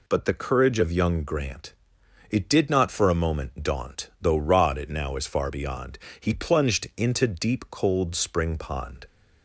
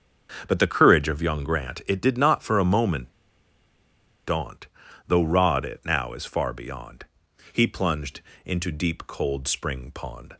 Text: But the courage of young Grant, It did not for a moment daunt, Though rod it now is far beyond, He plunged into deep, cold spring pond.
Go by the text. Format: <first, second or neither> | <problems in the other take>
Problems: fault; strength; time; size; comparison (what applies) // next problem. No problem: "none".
first | starts louder than the rest; until 1.4 s; 6.5 dB // pauses between "moment" and "daunt"; at 3.1 s; 1.1 s long // pauses between "plunged" and "into"; slight; at 8.2 s; 0.24 s long